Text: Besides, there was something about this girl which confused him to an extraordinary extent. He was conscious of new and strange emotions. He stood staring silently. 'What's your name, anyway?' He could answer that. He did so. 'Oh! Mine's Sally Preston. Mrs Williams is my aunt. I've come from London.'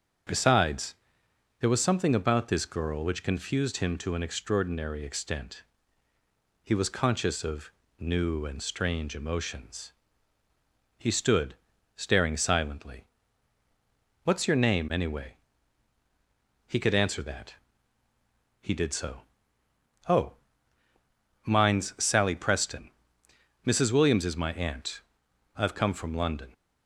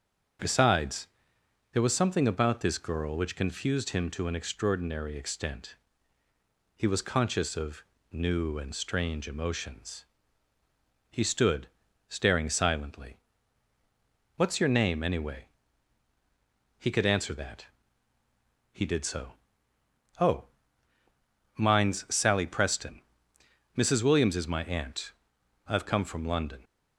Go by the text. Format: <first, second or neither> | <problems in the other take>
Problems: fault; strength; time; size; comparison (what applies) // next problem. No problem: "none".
neither | starts louder than the rest; strong; the same in both // pauses between "of" and "new"; slight; the same in both // pauses between "stood" and "staring"; the same in both